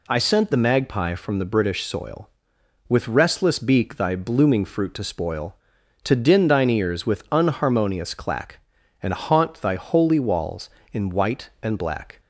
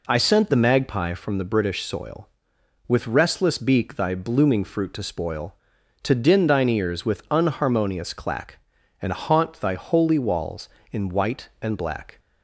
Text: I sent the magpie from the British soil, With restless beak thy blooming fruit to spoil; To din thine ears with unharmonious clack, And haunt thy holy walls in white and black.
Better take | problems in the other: first | starts louder than the rest; until 1.0 s; 3.5 dB

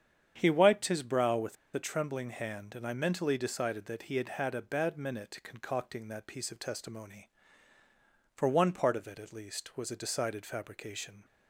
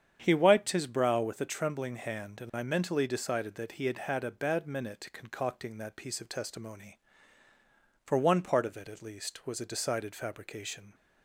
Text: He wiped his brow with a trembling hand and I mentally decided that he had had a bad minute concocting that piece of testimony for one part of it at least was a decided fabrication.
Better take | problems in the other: second | starts louder than the rest; strong; until 1.3 s; 8 dB; strong in the second // pauses between "with" and "a"; slight; at 1.5 s; 0.19 s long

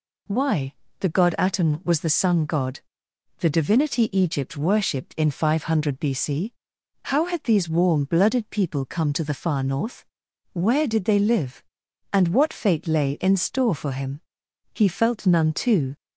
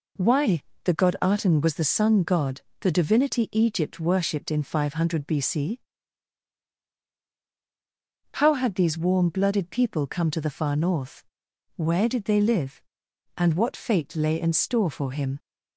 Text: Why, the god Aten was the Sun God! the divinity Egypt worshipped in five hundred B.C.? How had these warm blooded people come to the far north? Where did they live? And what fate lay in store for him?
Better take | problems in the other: second | goes on to say "He felt none too"; noticeable; from 14.7 s on; 1.2 s long

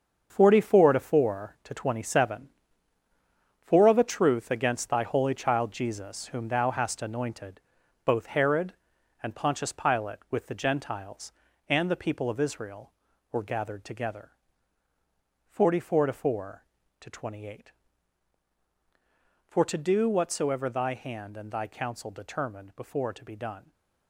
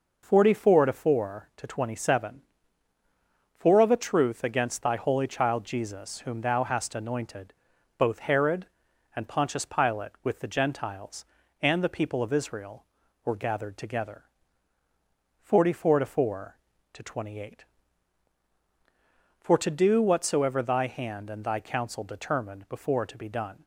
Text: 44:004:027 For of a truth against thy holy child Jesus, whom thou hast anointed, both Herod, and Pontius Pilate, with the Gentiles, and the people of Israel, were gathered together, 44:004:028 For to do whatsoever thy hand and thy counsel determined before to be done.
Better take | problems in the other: second | gets quieter; strong; throughout; 10 dB

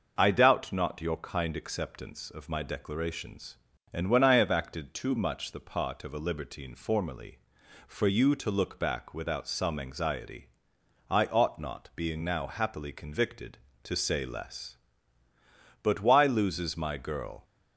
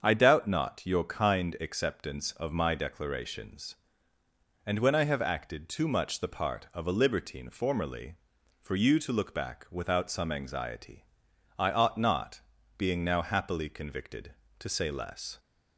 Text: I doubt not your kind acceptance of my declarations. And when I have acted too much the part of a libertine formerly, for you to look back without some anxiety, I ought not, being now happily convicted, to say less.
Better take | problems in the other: second | starts louder than the rest; noticeable; until 1.2 s; 6 dB; strong in the second // goes on to say "But why loses my girl"; from 15.8 s on; 1.6 s long

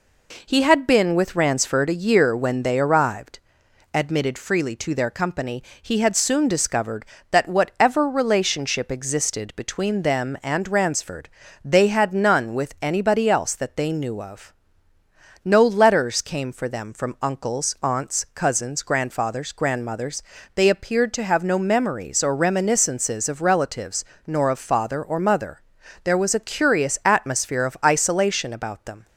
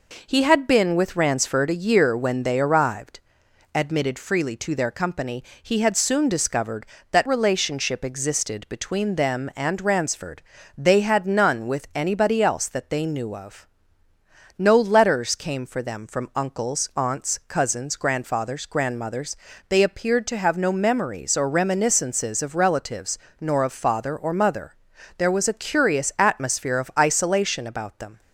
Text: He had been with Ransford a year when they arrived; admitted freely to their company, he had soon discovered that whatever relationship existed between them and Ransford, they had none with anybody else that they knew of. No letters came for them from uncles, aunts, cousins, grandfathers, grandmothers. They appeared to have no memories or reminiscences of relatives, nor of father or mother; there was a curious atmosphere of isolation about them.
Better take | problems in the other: first | skips "whatever"; at 7.2 s

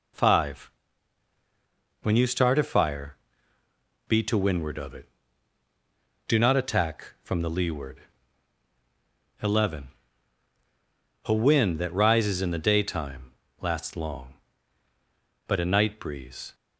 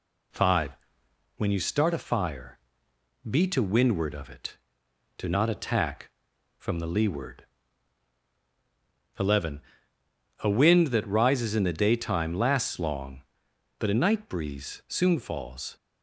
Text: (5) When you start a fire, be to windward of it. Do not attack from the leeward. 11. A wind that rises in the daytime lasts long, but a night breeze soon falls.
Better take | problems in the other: second | pauses between "daytime" and "lasts"; slight; at 13.3 s; 0.28 s long // stops before "soon falls"; at 16.5 s

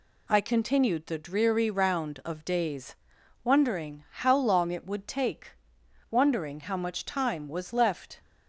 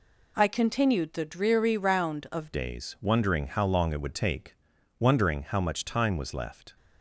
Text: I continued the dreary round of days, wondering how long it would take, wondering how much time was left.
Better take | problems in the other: first | changes voice at "days"; from 2.5 s on; 4.2 s long

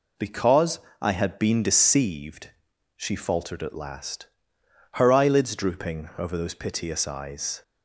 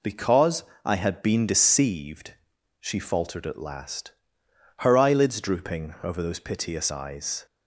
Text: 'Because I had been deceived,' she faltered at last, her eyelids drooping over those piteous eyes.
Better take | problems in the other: neither | pauses between "Because" and "I"; slight; the same in both

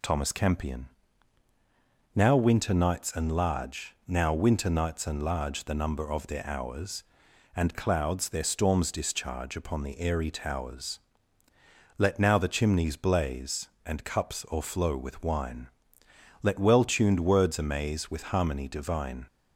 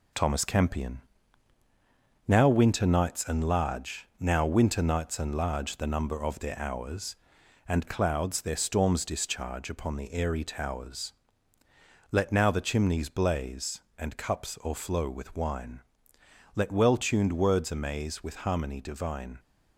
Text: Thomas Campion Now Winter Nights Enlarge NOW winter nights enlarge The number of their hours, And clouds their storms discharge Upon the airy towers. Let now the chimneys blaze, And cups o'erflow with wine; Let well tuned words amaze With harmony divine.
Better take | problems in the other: first | gets quieter; noticeable; throughout; 5.5 dB // pauses between "Campion" and "Now"; strong; at 0.9 s; 1.2 s long; strong in the first

